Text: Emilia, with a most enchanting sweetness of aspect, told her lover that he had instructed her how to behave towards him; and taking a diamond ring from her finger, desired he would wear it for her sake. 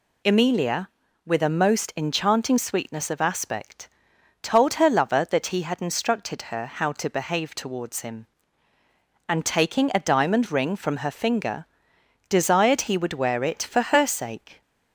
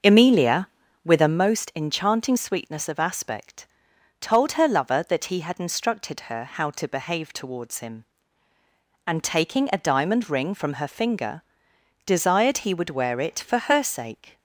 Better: first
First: none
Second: starts louder than the rest; until 1.4 s; 6.5 dB

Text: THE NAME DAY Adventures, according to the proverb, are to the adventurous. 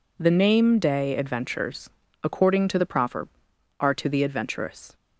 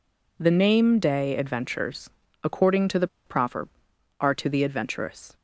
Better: first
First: none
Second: pauses between "the" and "proverb"; slight; at 3.0 s; 0.19 s long

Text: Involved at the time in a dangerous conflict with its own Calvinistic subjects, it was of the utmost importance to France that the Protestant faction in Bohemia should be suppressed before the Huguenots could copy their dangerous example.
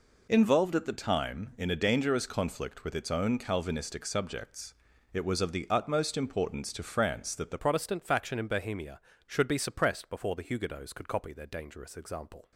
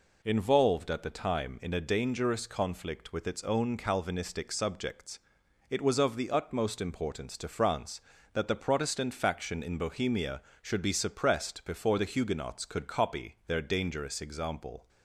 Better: second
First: changes voice at "Protestant"; from 7.5 s on; 5.0 s long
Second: none

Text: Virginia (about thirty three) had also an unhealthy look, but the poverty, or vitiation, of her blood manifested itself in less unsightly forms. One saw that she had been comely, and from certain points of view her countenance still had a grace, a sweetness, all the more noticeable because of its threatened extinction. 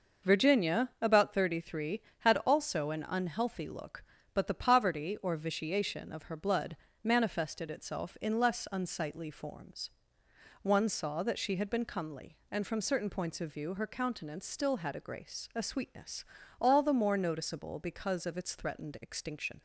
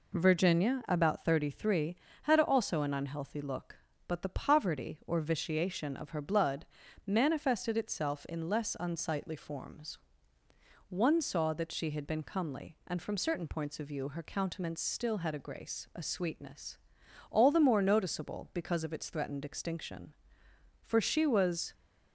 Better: first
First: pauses between "blood" and "manifested"; slight; at 6.7 s; 0.30 s long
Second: pauses between "blood" and "manifested"; at 6.6 s; 0.40 s long // goes on to say "For she was"; noticeable; from 20.8 s on; 0.90 s long

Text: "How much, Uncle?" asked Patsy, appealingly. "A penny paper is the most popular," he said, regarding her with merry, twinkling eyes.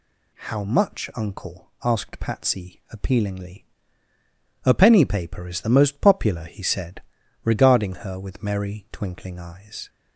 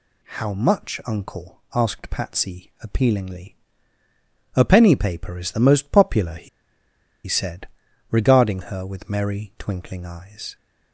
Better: first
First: none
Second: pauses between "he" and "said"; noticeable; at 6.4 s; 0.78 s long

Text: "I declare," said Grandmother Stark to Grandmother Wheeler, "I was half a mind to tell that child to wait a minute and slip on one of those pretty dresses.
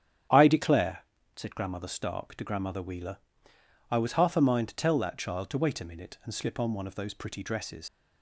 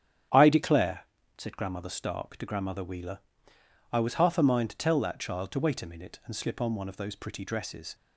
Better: second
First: starts louder than the rest; strong; until 1.6 s; 9.5 dB // leaves "dresses" unfinished; at 7.8 s; 50 ms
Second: starts louder than the rest; strong; until 1.6 s; 9.5 dB

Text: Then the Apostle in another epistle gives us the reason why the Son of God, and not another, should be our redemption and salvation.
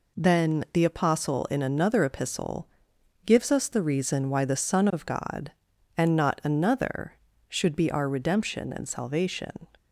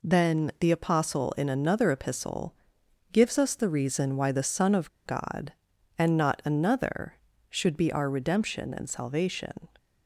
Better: first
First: pauses between "epistle" and "gives"; noticeable; at 2.6 s; 0.58 s long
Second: pauses between "epistle" and "gives"; noticeable; at 2.5 s; 0.58 s long // pauses between "of" and "God"; slight; at 4.8 s; 0.17 s long

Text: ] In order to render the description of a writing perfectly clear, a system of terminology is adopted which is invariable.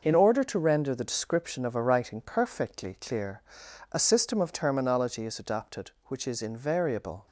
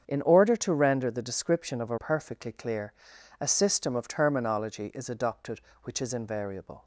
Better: first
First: none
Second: starts louder than the rest; strong; until 1.0 s; 7.5 dB // skips "writing"; at 1.9 s

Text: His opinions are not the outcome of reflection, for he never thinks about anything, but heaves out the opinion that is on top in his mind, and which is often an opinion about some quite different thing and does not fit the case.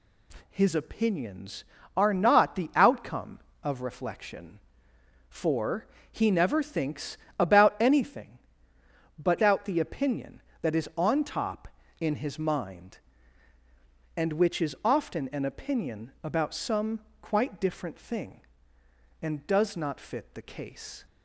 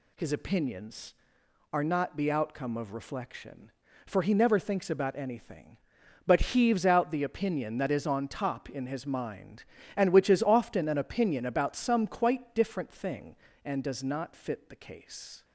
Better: second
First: pauses between "for" and "he"; slight; at 5.8 s; 0.26 s long // pauses between "thinks" and "about"; slight; at 7.1 s; 0.22 s long // skips "heaves"; at 9.4 s // pauses between "some" and "quite"; slight; at 16.9 s; 0.22 s long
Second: none

